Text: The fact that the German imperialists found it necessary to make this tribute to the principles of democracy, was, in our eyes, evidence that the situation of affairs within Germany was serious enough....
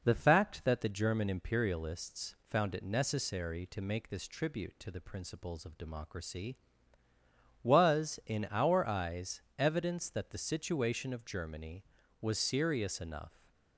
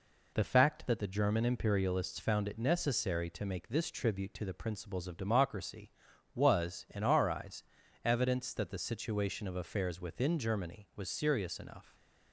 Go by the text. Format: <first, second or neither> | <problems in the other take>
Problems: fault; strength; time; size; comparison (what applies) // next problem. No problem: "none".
second | skips "affairs within"; at 11.2 s